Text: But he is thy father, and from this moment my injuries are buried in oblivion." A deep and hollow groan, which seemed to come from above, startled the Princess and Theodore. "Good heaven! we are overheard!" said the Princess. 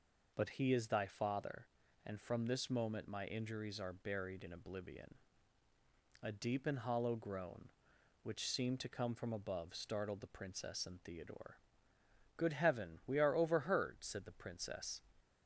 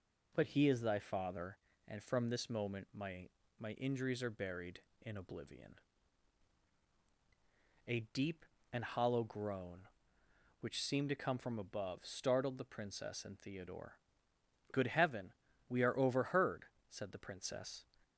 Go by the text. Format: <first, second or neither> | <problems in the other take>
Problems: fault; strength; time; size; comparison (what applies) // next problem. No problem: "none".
first | says "my" twice; at 3.5 s